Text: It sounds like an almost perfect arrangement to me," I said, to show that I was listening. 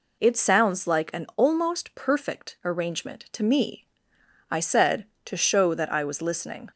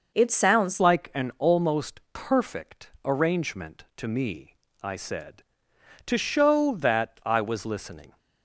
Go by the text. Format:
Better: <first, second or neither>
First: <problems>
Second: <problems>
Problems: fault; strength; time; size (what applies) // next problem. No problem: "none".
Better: first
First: none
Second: changes voice at "like"; from 0.7 s on; 7.4 s long